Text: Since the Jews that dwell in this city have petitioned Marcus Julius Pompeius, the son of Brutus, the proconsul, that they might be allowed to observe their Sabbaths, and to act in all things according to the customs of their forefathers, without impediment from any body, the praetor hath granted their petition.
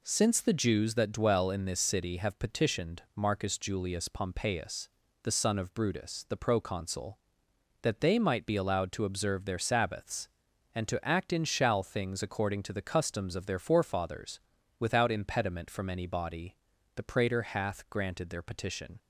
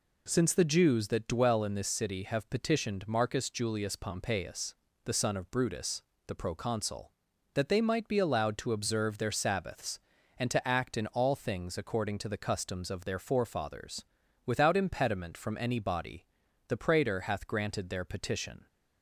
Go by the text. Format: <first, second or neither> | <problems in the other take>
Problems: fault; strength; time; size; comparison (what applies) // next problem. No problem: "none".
second | says "shall" for "all"; at 11.4 s